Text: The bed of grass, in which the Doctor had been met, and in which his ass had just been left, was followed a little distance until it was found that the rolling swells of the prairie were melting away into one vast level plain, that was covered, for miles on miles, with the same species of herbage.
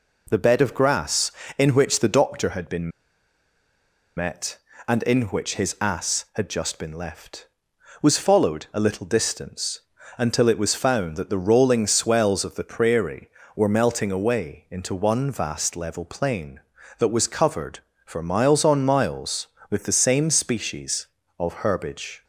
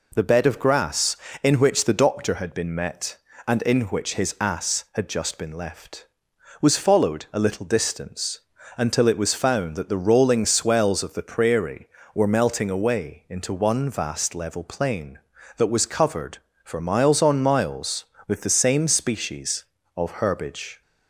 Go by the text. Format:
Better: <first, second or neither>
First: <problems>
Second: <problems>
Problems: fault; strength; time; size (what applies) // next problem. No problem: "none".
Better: second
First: pauses between "been" and "met"; strong; at 2.8 s; 1.2 s long // pauses between "distance" and "until"; at 9.7 s; 0.38 s long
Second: pauses between "distance" and "until"; at 8.3 s; 0.38 s long